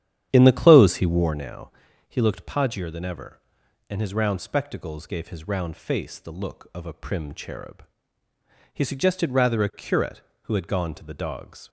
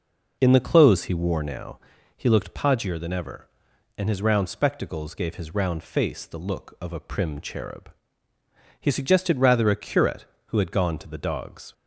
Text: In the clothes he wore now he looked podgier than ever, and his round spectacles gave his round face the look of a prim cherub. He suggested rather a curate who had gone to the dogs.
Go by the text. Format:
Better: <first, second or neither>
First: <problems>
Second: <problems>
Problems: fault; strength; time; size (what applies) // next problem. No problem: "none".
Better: second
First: starts louder than the rest; strong; until 1.4 s; 10 dB // pauses between "now" and "he"; slight; at 1.7 s; 0.36 s long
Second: pauses between "now" and "he"; slight; at 1.8 s; 0.36 s long